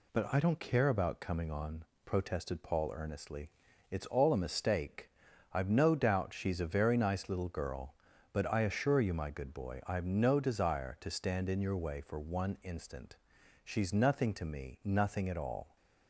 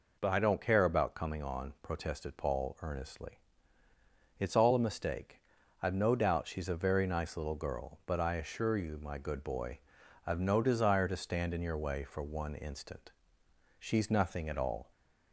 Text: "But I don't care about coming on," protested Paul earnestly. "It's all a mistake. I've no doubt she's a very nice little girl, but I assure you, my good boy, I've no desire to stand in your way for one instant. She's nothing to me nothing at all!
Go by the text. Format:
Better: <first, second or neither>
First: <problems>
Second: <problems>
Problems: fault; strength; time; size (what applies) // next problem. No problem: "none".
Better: first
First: none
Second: skips "to me nothing"; at 14.4 s